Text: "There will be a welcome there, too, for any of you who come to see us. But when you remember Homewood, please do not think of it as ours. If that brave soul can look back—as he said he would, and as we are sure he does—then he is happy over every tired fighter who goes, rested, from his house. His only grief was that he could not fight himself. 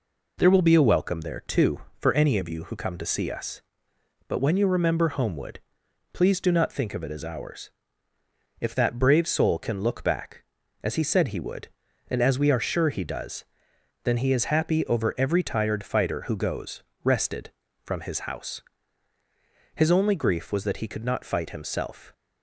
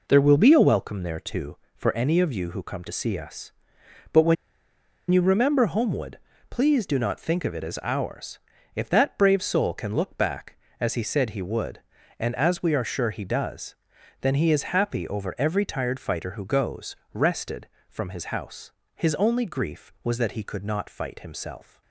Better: first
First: none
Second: pauses between "when" and "you"; noticeable; at 4.3 s; 0.76 s long

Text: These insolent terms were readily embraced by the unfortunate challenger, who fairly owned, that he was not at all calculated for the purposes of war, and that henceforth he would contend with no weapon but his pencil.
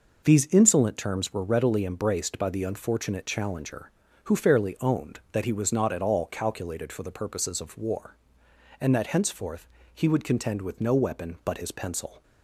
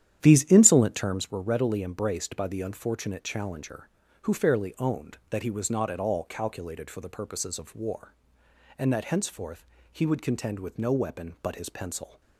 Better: first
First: pauses between "henceforth" and "he"; slight; at 9.6 s; 0.26 s long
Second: starts louder than the rest; strong; until 1.2 s; 10.5 dB // pauses between "henceforth" and "he"; slight; at 9.6 s; 0.26 s long

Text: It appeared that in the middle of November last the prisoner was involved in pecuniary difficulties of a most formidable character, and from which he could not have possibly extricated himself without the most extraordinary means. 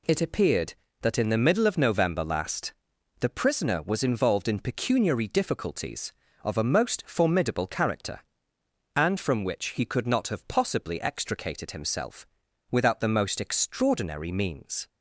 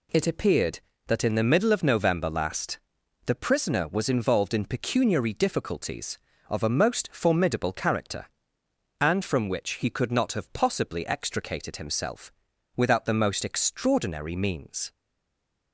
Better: first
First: pauses between "last" and "the"; noticeable; at 2.7 s; 0.46 s long // pauses between "himself" and "without"; at 12.2 s; 0.44 s long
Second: pauses between "last" and "the"; noticeable; at 2.8 s; 0.46 s long // pauses between "himself" and "without"; at 12.3 s; 0.44 s long // stays silent after the last word; slight; from 14.9 s on; 0.8 s long

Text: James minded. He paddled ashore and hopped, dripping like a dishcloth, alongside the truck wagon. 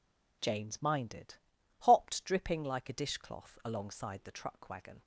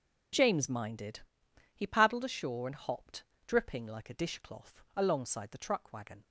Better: second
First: skips "He paddled ashore and"; at 1.5 s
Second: none

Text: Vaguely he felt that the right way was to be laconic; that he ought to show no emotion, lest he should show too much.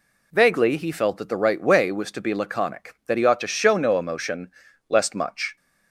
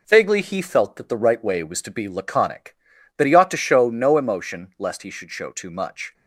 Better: second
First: skips "he should show too"; at 5.1 s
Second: none

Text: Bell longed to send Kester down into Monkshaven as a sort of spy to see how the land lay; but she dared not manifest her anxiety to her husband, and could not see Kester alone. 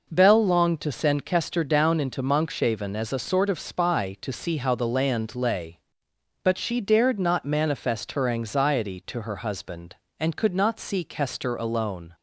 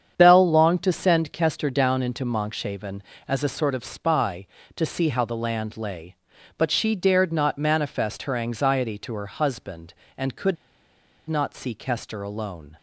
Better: first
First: none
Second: starts louder than the rest; strong; until 1.1 s; 8 dB // pauses between "could" and "not"; noticeable; at 10.5 s; 0.72 s long

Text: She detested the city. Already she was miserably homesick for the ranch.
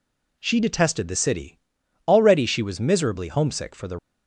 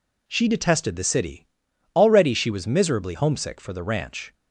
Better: second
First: stops before "ranch"; at 3.9 s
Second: none

